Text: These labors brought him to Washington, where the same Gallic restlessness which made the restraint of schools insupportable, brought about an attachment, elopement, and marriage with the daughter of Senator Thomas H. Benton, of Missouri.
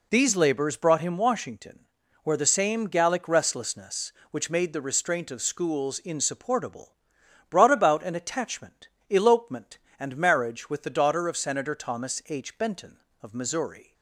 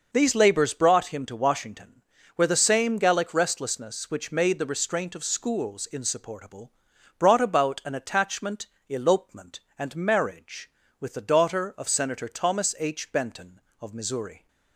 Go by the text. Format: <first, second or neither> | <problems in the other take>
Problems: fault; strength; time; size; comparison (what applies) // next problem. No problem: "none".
second | skips "to"; at 1.1 s